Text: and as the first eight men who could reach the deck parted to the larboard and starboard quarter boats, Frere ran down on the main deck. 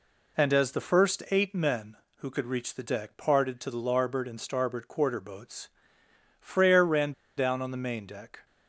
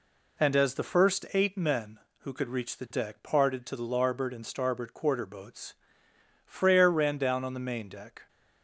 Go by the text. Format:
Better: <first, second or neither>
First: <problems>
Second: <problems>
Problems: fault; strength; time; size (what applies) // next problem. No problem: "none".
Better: second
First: pauses between "ran" and "down"; slight; at 7.1 s; 0.25 s long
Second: none